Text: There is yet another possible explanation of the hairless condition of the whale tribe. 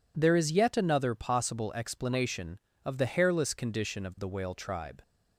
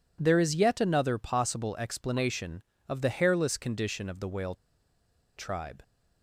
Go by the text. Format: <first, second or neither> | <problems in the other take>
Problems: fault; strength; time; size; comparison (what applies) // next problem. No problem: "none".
first | pauses between "whale" and "tribe"; noticeable; at 4.5 s; 0.81 s long